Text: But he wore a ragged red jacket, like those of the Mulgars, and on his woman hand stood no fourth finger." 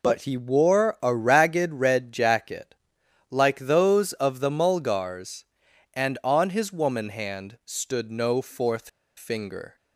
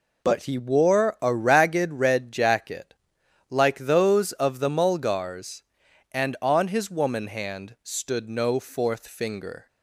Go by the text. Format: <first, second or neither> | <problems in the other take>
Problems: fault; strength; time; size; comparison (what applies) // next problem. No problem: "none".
second | pauses between "fourth" and "finger"; slight; at 8.8 s; 0.27 s long